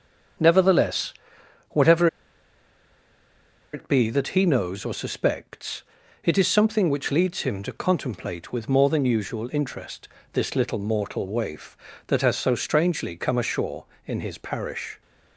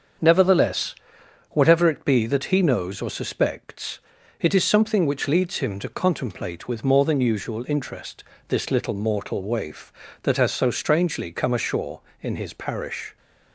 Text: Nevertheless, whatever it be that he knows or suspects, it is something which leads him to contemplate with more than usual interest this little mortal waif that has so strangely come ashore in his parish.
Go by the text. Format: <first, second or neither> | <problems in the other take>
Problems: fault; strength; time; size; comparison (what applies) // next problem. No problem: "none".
second | starts louder than the rest; until 1.9 s; 7 dB; also in the second // pauses between "whatever" and "it"; strong; at 2.0 s; 1.6 s long // pauses between "interest" and "this"; slight; at 10.0 s; 0.24 s long; slight in the second